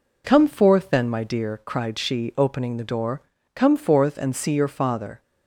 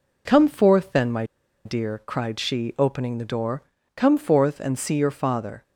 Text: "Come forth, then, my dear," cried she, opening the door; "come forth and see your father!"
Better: first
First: none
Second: pauses between "my" and "dear"; at 1.2 s; 0.41 s long

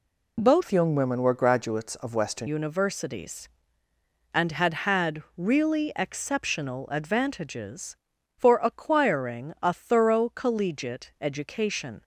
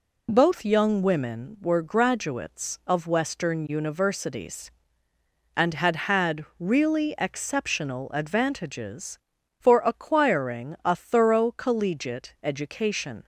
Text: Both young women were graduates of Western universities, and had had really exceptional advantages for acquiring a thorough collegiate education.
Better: second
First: changes voice from "young" to "Western"; from 0.7 to 2.4 s; 1.7 s long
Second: none

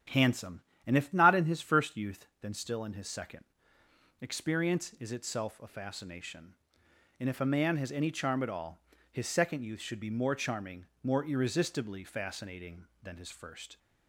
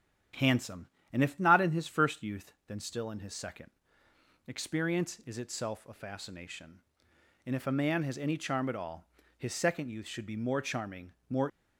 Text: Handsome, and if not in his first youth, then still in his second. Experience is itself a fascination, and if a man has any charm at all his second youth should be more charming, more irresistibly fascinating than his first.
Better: first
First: starts louder than the rest; strong; until 1.3 s; 10 dB // pauses between "all" and "his"; slight; at 8.8 s; 0.30 s long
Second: starts louder than the rest; strong; until 1.6 s; 10 dB // pauses between "all" and "his"; slight; at 9.0 s; 0.30 s long // stops before "irresistibly fascinating than his first"; at 11.4 s

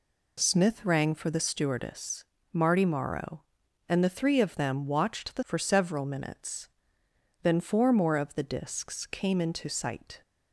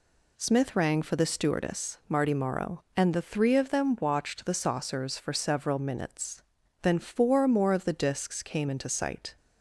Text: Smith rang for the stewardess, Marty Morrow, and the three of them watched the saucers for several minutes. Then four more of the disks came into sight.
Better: second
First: skips "saucers"; at 5.4 s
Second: none

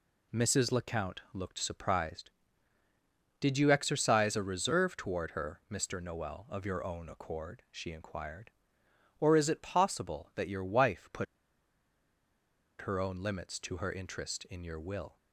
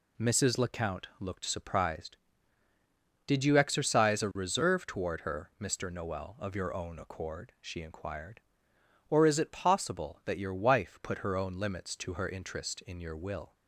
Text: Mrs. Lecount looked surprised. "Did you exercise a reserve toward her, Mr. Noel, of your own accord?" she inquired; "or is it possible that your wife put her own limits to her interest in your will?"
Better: second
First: pauses between "put" and "her"; strong; at 11.2 s; 1.5 s long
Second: none

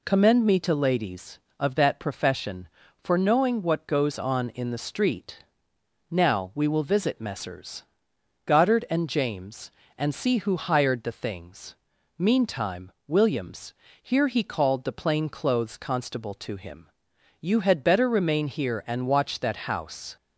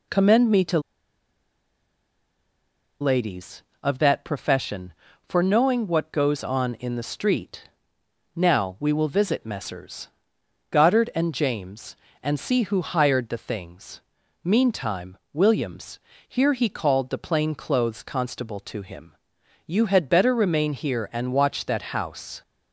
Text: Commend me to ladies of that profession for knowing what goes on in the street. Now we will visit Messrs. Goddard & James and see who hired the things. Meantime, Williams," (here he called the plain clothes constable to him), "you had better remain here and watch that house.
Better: first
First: pauses between "Messrs" and "Goddard"; noticeable; at 7.8 s; 0.60 s long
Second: pauses between "to" and "ladies"; strong; at 0.7 s; 2.2 s long // pauses between "Messrs" and "Goddard"; noticeable; at 10.0 s; 0.60 s long

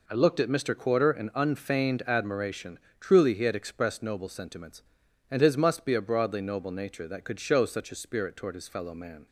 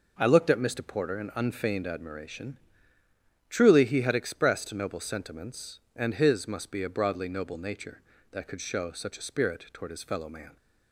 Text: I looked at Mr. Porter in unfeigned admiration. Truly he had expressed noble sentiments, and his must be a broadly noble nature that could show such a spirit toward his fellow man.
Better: second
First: says "Quarter" for "Porter"; at 0.7 s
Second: none

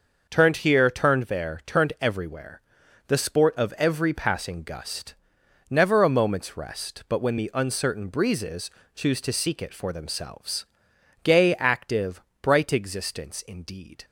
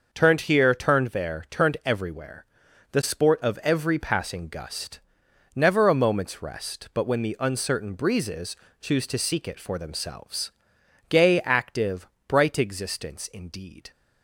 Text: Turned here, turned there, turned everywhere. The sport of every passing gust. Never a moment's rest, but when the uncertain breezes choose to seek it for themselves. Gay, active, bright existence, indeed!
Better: neither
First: starts louder than the rest; until 1.3 s; 6 dB // pauses between "breezes" and "choose"; slight; at 8.6 s; 0.26 s long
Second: starts louder than the rest; until 1.1 s; 6 dB // pauses between "breezes" and "choose"; slight; at 8.5 s; 0.26 s long

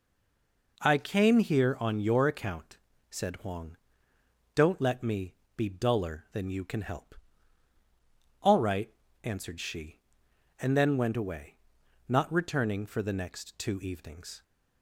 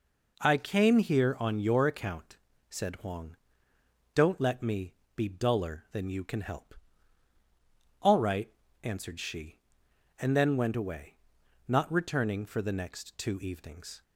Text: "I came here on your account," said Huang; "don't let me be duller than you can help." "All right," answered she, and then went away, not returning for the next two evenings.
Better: second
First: stays silent before the first word; slight; until 0.7 s; 0.7 s long // pauses between "me" and "be"; slight; at 5.3 s; 0.20 s long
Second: pauses between "me" and "be"; slight; at 4.9 s; 0.20 s long

